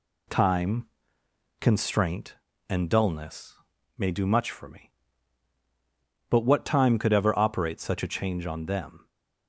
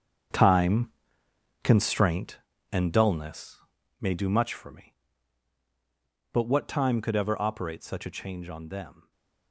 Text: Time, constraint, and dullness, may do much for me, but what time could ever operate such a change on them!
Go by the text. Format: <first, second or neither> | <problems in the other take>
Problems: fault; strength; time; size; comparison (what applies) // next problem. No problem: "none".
first | gets quieter; strong; throughout; 12 dB // stays silent after the last word; slight; from 9.0 s on; 0.5 s long